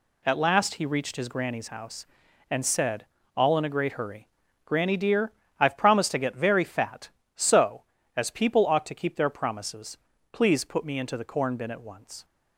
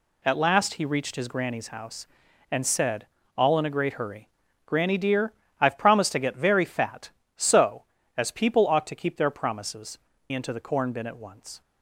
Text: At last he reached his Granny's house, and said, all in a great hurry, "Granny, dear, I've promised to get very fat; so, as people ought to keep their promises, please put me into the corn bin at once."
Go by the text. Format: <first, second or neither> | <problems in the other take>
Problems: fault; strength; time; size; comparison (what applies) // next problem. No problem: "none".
first | skips "please put me"; at 10.1 s